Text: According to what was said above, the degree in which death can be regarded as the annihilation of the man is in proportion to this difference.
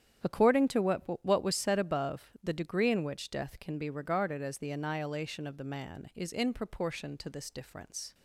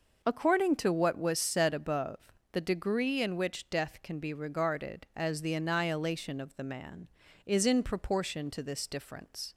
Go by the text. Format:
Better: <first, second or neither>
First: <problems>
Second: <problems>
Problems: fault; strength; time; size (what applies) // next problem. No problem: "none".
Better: second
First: starts louder than the rest; strong; until 1.4 s; 9.5 dB // says "what" twice; at 1.2 s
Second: none